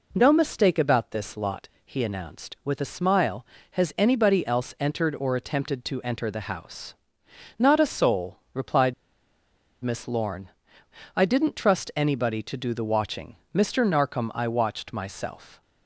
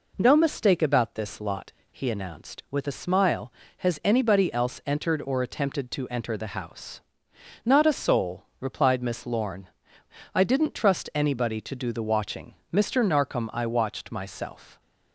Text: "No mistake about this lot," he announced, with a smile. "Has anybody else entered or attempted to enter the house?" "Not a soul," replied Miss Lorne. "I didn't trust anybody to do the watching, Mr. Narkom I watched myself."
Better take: second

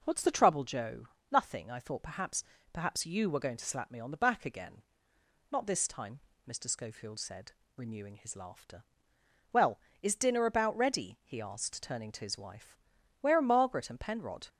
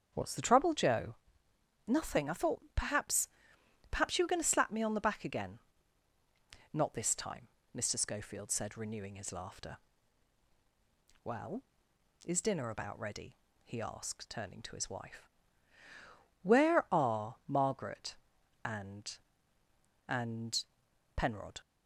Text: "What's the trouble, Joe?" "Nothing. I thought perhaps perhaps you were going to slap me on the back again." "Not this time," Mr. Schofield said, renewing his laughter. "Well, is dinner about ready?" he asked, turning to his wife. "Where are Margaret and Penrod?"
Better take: first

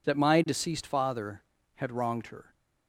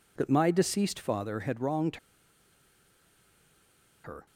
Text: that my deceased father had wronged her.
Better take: first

